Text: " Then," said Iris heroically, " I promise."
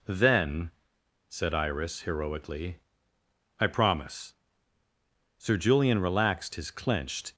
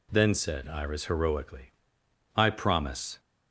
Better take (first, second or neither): second